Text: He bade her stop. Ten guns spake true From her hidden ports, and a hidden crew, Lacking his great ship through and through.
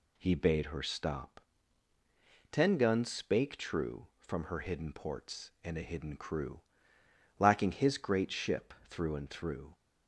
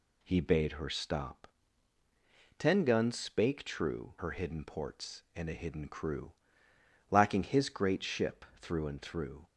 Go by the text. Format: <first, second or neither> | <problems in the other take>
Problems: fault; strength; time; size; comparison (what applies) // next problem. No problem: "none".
first | skips "From"; at 4.1 s